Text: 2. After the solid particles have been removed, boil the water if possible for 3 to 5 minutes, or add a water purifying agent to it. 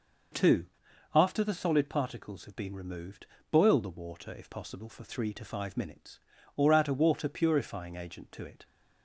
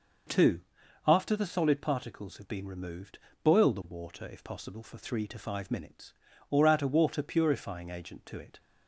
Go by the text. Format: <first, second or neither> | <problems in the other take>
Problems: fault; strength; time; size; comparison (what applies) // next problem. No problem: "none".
neither | none